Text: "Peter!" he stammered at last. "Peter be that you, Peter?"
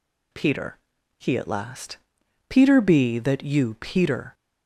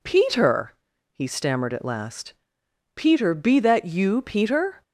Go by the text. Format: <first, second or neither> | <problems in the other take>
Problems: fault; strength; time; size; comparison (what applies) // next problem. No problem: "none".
second | skips "stammered"; at 1.3 s